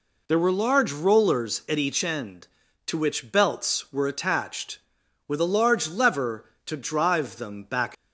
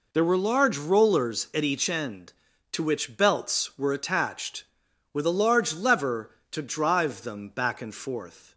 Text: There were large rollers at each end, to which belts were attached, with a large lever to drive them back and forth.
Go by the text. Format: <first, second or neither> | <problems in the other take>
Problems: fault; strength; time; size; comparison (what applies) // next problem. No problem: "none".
second | stops before "and forth"; at 7.9 s